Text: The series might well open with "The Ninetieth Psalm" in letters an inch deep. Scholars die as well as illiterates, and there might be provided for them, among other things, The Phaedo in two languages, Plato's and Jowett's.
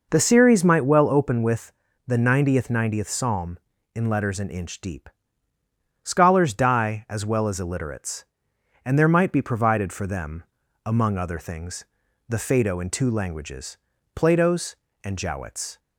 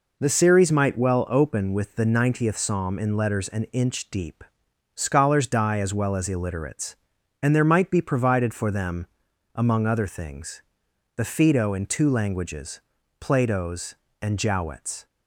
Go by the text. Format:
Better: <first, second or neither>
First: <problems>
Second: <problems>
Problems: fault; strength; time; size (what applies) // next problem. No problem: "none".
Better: second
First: pauses between "with" and "The"; slight; at 1.7 s; 0.36 s long // says "Ninetieth" twice; at 2.7 s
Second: none